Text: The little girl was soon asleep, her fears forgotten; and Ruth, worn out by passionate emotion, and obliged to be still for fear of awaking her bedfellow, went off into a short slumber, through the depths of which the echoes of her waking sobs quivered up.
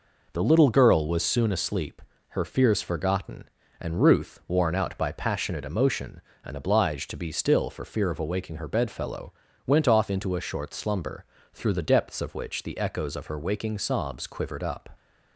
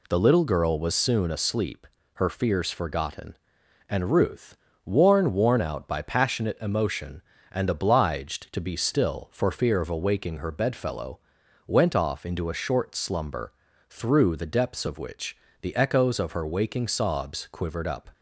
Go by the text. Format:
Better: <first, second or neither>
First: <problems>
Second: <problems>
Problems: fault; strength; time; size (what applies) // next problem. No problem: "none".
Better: first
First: none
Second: says "worn" twice; at 5.3 s // pauses between "which" and "the"; slight; at 15.3 s; 0.24 s long